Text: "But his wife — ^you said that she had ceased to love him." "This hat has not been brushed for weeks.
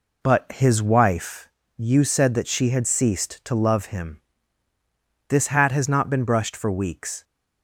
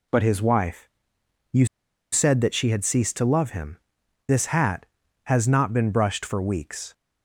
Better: first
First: none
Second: pauses between "you" and "said"; noticeable; at 1.6 s; 0.46 s long

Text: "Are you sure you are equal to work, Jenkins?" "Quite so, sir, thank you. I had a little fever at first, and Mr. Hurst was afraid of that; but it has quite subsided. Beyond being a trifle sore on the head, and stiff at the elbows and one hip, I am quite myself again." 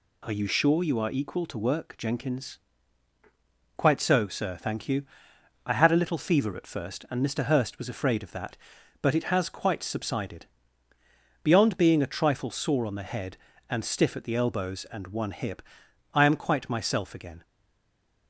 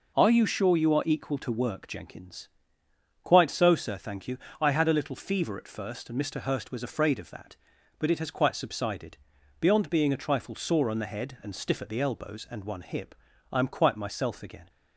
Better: second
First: stays silent after the last word; slight; from 17.4 s on; 0.8 s long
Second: none

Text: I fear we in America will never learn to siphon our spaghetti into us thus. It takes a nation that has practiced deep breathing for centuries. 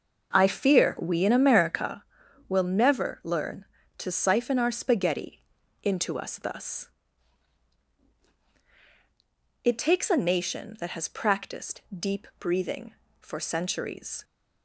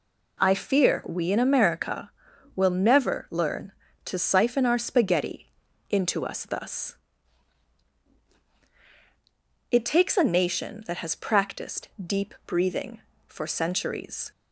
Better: second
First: starts louder than the rest; noticeable; until 2.0 s; 6 dB // pauses between "spaghetti" and "into"; at 5.4 s; 0.42 s long // pauses between "practiced" and "deep"; slight; at 11.8 s; 0.16 s long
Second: pauses between "spaghetti" and "into"; at 5.4 s; 0.42 s long // pauses between "practiced" and "deep"; slight; at 11.8 s; 0.16 s long

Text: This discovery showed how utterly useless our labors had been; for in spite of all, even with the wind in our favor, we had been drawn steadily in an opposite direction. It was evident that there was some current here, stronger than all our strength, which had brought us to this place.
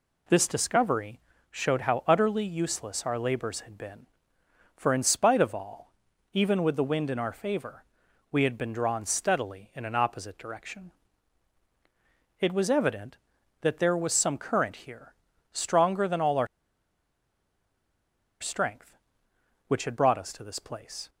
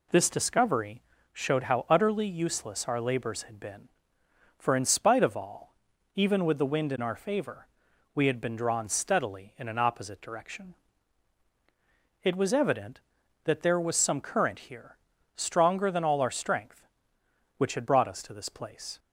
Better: second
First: pauses between "discovery" and "showed"; slight; at 1.2 s; 0.28 s long // pauses between "our" and "strength"; strong; at 16.4 s; 1.9 s long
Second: pauses between "discovery" and "showed"; slight; at 1.0 s; 0.28 s long

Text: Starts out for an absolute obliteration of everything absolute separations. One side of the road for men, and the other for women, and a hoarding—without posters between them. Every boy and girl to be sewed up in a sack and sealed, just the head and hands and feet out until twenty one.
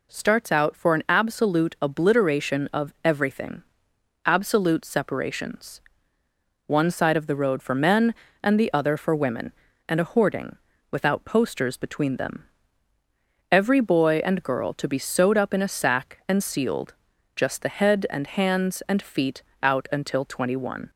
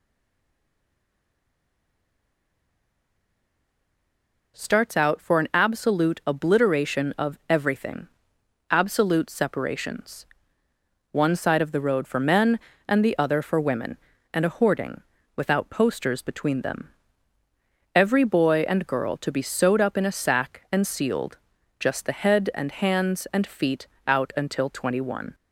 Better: first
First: pauses between "everything" and "absolute"; noticeable; at 3.6 s; 0.62 s long // pauses between "feet" and "out"; slight; at 19.4 s; 0.20 s long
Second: stays silent before the first word; strong; until 4.5 s; 4.5 s long // pauses between "everything" and "absolute"; noticeable; at 8.0 s; 0.62 s long // pauses between "feet" and "out"; slight; at 23.8 s; 0.20 s long

